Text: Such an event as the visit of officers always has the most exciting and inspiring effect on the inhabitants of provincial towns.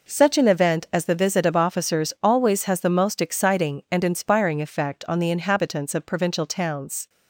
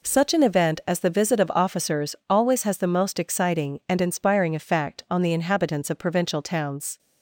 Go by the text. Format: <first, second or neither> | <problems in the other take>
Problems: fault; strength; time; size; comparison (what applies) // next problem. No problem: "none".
neither | none